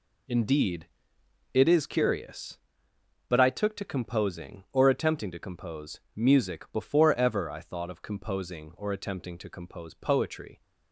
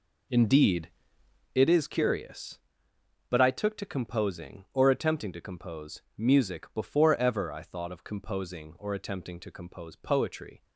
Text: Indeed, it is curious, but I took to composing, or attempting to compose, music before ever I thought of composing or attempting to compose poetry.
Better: first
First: none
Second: starts louder than the rest; until 1.5 s; 3.5 dB

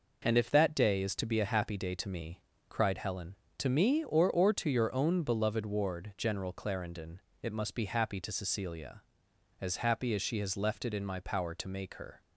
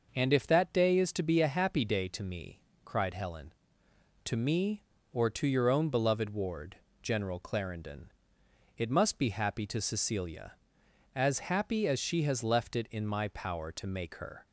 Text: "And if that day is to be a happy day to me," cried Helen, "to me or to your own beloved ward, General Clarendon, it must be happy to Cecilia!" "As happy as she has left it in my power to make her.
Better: second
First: says "or" twice; at 4.3 s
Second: none

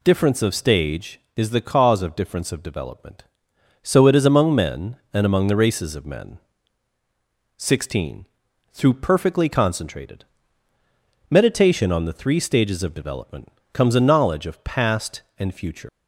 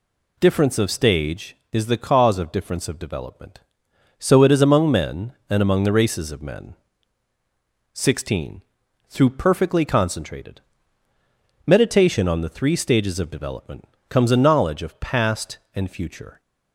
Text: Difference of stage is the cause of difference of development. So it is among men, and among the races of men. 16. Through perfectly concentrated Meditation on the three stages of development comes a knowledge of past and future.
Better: second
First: pauses between "concentrated" and "Meditation"; at 10.2 s; 1.0 s long // pauses between "development" and "comes"; slight; at 13.5 s; 0.22 s long // leaves "future" unfinished; at 15.8 s; 145 ms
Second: pauses between "concentrated" and "Meditation"; at 10.5 s; 1.0 s long // pauses between "development" and "comes"; slight; at 13.8 s; 0.22 s long

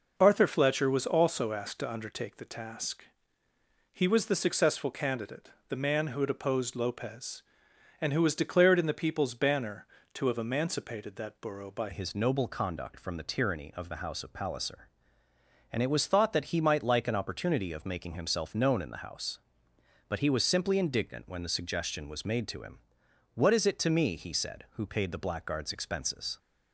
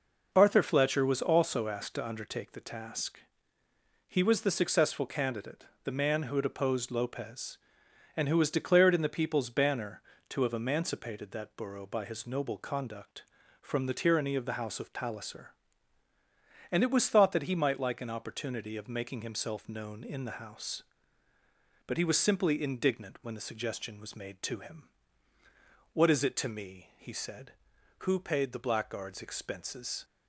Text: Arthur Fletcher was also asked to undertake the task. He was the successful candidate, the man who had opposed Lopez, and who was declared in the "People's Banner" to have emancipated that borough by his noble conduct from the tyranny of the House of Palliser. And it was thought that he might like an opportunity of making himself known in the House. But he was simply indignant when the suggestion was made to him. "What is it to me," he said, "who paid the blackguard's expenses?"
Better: second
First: changes voice at "his"; from 11.9 s on; 14.4 s long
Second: none

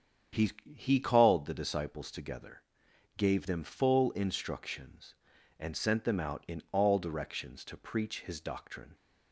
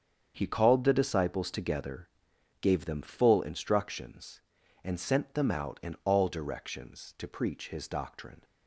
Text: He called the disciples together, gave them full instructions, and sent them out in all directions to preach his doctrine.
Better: second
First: starts louder than the rest; strong; until 1.5 s; 8 dB // says "He" twice; at 0.7 s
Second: starts louder than the rest; strong; until 1.3 s; 7.5 dB

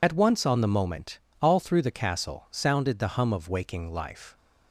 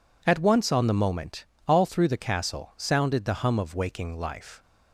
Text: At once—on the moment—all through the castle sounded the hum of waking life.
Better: second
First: loses the start of "At"; at 0.0 s; 50 ms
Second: none

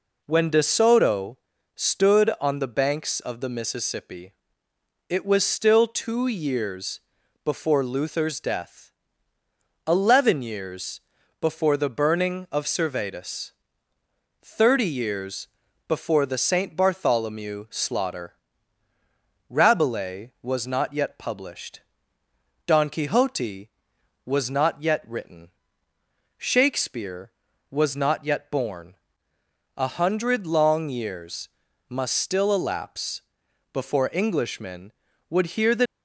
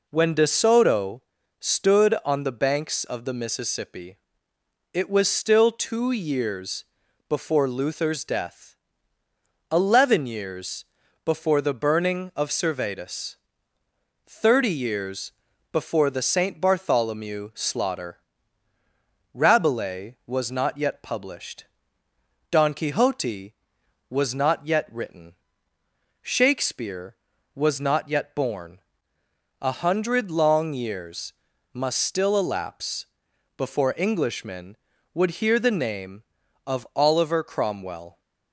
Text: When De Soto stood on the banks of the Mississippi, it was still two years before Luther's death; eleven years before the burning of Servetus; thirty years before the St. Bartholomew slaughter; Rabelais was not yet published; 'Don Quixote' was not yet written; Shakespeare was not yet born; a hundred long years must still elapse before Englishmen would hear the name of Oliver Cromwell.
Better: second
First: pauses between "Soto" and "stood"; at 1.3 s; 0.38 s long // pauses between "years" and "before"; at 7.0 s; 0.42 s long // pauses between "years" and "before"; at 11.0 s; 0.40 s long // pauses between "years" and "before"; at 15.4 s; 0.40 s long // pauses between "years" and "must"; at 31.4 s; 0.40 s long // pauses between "elapse" and "before"; noticeable; at 33.2 s; 0.50 s long // stops before "name of Oliver Cromwell"; at 35.8 s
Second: pauses between "Soto" and "stood"; at 1.2 s; 0.38 s long // pauses between "years" and "before"; at 6.8 s; 0.42 s long // pauses between "years" and "before"; at 10.8 s; 0.40 s long // pauses between "years" and "before"; at 15.3 s; 0.40 s long // pauses between "years" and "must"; at 31.3 s; 0.40 s long // pauses between "elapse" and "before"; noticeable; at 33.0 s; 0.50 s long

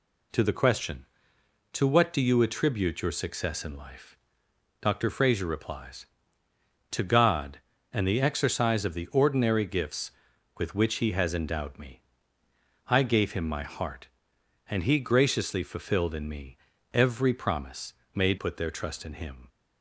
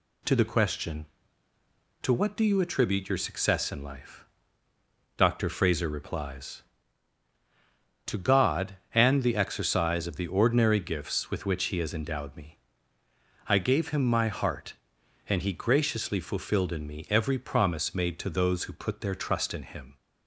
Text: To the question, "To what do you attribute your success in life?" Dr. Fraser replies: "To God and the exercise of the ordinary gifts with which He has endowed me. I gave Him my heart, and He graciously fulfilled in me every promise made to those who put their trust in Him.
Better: second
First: pauses between "me" and "every"; slight; at 16.5 s; 0.36 s long // pauses between "promise" and "made"; slight; at 17.9 s; 0.20 s long // skips "to those who"; at 18.3 s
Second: none

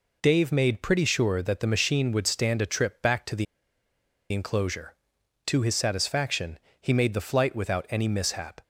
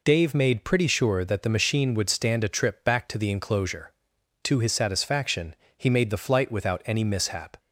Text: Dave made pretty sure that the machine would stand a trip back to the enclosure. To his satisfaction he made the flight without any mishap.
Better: second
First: pauses between "the" and "enclosure"; noticeable; at 3.4 s; 0.87 s long // pauses between "satisfaction" and "he"; slight; at 6.5 s; 0.24 s long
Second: pauses between "satisfaction" and "he"; slight; at 5.5 s; 0.24 s long

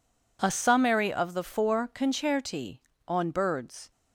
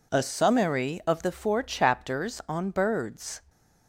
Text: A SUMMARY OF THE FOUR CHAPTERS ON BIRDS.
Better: second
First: says "Concerti" for "CHAPTERS"; at 1.9 s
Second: none

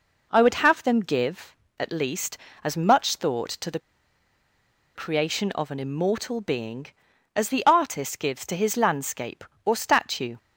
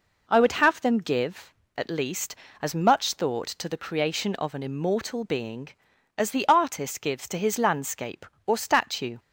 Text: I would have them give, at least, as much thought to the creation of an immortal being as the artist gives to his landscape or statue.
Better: second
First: pauses between "the" and "creation"; at 3.7 s; 1.1 s long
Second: none

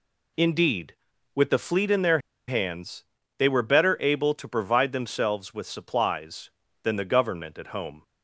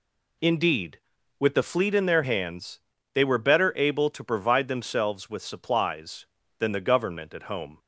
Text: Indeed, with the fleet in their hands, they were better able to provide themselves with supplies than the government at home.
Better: second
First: pauses between "their" and "hands"; slight; at 2.1 s; 0.30 s long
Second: none

